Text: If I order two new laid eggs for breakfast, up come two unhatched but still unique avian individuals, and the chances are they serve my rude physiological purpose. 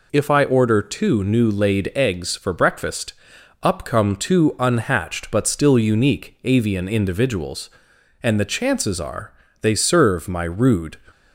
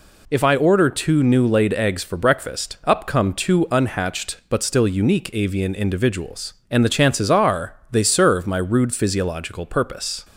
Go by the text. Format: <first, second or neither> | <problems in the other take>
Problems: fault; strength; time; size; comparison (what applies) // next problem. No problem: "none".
second | pauses between "are" and "they"; slight; at 9.3 s; 0.28 s long; slight in the second // stops before "physiological purpose"; at 11.1 s